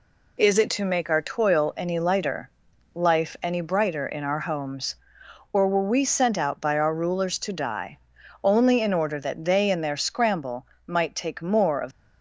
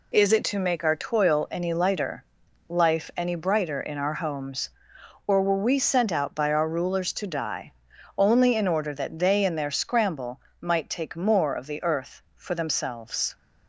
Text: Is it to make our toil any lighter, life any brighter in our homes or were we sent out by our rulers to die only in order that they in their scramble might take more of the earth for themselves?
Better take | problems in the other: second | pauses between "die" and "only"; at 7.9 s; 0.42 s long; also in the second // pauses between "scramble" and "might"; slight; at 10.6 s; 0.22 s long; slight in the second // stops before "the earth for themselves"; at 11.9 s

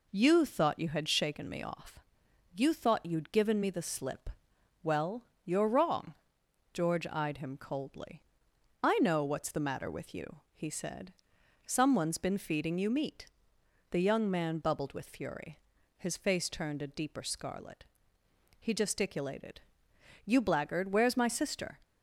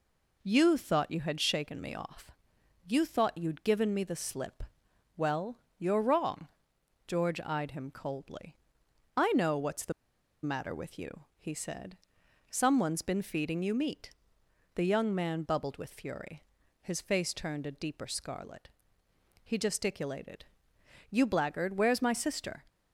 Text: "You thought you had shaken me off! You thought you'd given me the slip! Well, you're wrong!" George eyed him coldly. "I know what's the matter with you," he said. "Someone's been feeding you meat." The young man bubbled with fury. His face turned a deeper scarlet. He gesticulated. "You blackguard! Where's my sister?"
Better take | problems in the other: first | pauses between "the" and "matter"; noticeable; at 9.9 s; 0.51 s long

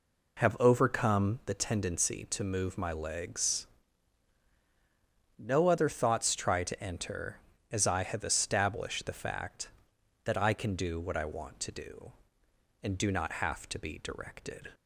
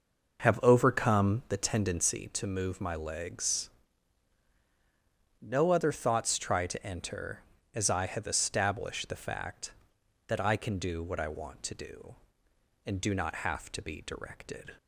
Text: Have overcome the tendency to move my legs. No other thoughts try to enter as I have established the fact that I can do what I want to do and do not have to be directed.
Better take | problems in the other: first | starts louder than the rest; noticeable; until 2.3 s; 6 dB

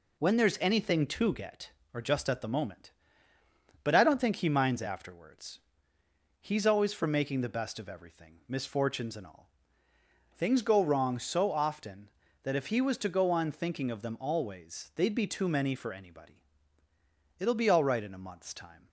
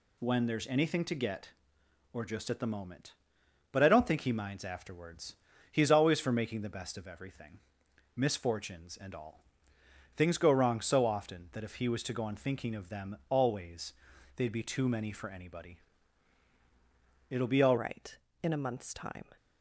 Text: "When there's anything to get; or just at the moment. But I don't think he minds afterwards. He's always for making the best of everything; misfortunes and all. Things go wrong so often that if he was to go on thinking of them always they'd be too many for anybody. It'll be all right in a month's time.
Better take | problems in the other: first | pauses between "always" and "they'd"; noticeable; at 13.9 s; 0.46 s long // changes voice at "right"; from 17.7 s on; 1.5 s long

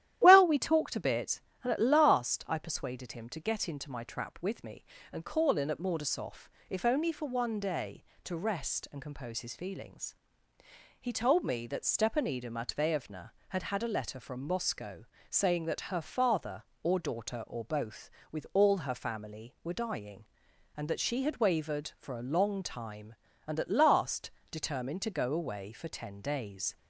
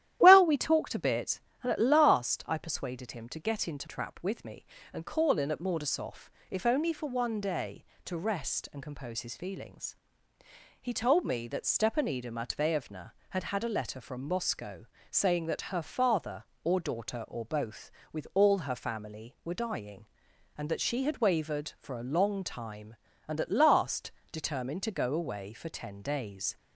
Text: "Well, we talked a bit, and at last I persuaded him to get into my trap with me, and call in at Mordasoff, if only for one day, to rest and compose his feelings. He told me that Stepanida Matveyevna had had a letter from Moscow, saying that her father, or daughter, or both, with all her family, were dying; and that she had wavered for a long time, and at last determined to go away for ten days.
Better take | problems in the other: first | starts louder than the rest; strong; until 1.2 s; 12.5 dB; strong in the first // skips "my"; at 3.8 s // pauses between "last" and "determined"; slight; at 24.1 s; 0.22 s long; slight in the first

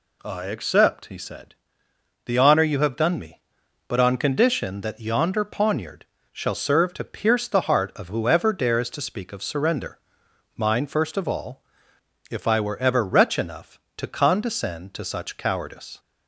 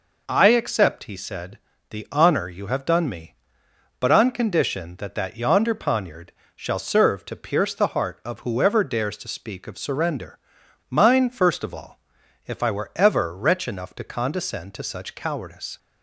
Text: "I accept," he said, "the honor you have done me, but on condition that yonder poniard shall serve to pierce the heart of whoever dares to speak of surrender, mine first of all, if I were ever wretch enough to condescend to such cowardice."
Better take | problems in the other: first | says "that" twice; at 5.1 s // pauses between "poniard" and "shall"; slight; at 6.3 s; 0.24 s long; slight in the first

